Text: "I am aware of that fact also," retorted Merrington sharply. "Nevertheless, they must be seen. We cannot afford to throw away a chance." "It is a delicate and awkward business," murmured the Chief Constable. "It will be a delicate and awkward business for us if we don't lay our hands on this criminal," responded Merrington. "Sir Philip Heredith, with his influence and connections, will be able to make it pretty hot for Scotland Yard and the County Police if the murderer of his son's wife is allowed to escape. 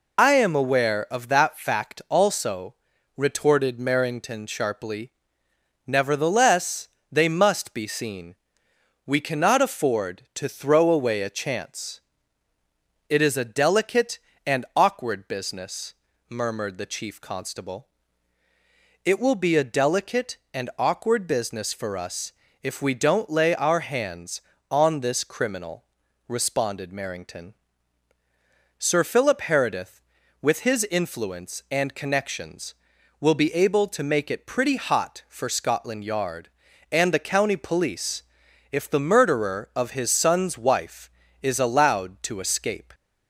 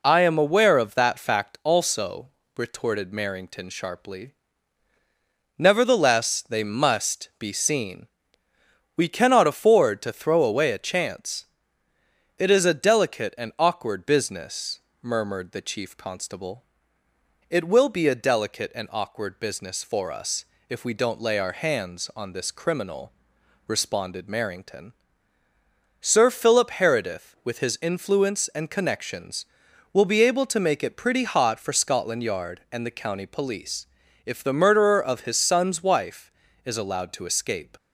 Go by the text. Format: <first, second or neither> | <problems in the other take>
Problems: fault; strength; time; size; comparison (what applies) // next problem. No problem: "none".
second | loses the start of "I"; at 0.1 s; 55 ms // pauses between "us" and "if"; slight; at 22.3 s; 0.30 s long; slight in the second // pauses between "Police" and "if"; noticeable; at 38.2 s; 0.48 s long; slight in the second